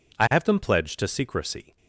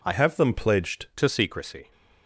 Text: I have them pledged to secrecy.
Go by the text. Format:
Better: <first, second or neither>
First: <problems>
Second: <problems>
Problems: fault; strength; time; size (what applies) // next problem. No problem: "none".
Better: first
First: none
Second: changes voice from "have" to "pledged"; from 0.1 to 1.0 s; 0.9 s long